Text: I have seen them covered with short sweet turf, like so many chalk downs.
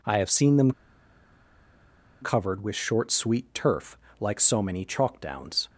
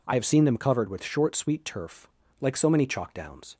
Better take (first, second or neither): second